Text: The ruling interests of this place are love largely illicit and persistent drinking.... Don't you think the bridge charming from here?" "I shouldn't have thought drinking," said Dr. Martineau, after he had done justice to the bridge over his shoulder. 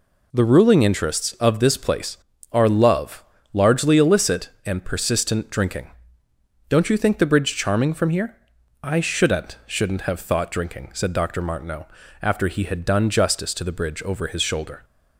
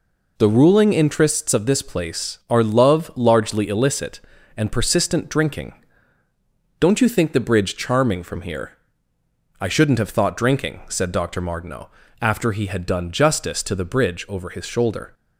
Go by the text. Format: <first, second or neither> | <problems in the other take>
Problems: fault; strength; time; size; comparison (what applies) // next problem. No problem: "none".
second | pauses between "love" and "largely"; slight; at 3.2 s; 0.28 s long // says "shouldn't" twice; at 9.6 s